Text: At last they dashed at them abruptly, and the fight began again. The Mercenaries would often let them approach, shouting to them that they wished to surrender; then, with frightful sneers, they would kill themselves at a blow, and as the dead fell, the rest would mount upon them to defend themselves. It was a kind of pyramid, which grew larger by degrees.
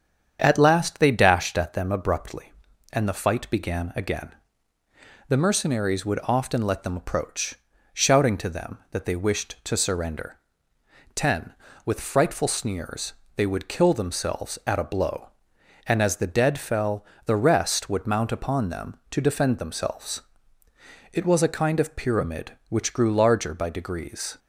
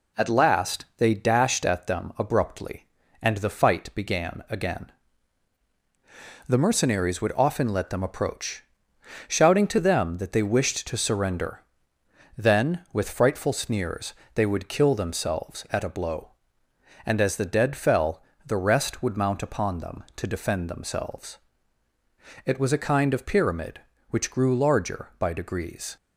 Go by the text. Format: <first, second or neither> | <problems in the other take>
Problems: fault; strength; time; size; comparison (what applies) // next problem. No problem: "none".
second | starts louder than the rest; strong; until 1.4 s; 8 dB // says "ten" for "then"; at 11.1 s